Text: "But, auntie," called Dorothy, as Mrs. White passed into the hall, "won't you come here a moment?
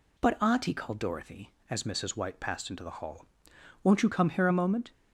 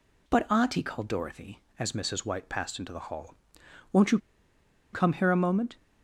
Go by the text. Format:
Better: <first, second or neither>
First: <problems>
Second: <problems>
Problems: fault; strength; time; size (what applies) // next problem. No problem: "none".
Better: first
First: none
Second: pauses between "you" and "come"; noticeable; at 4.1 s; 0.74 s long